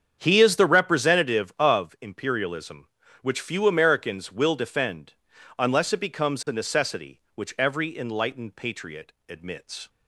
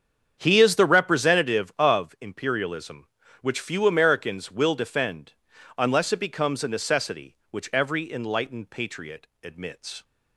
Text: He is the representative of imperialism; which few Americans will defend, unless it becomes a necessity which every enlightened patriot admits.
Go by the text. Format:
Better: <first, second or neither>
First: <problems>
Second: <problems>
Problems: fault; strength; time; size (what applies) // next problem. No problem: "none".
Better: neither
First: starts louder than the rest; strong; until 1.2 s; 7.5 dB // pauses between "patriot" and "admits"; slight; at 9.1 s; 0.16 s long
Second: starts louder than the rest; strong; until 1.3 s; 7.5 dB // pauses between "patriot" and "admits"; slight; at 9.2 s; 0.16 s long